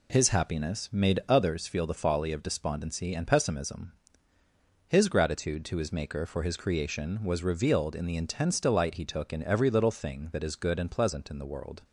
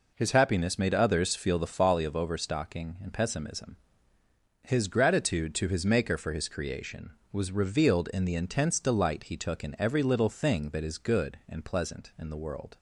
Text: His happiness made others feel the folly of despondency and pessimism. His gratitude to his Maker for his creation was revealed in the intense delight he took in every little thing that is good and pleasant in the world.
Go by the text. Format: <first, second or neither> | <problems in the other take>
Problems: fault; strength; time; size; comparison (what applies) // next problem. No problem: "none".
first | says "overstocking" for "despondency"; at 2.1 s